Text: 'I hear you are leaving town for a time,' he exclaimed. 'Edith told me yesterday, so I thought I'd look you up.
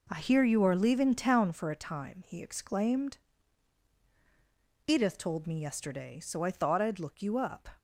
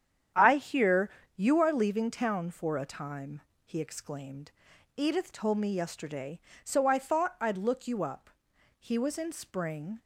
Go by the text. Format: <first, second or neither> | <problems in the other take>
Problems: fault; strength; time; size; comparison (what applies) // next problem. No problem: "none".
first | starts louder than the rest; strong; until 1.6 s; 9 dB // pauses between "hear" and "you"; slight; at 1.0 s; 0.26 s long // goes on to say "He was in spring"; noticeable; from 8.7 s on; 1.2 s long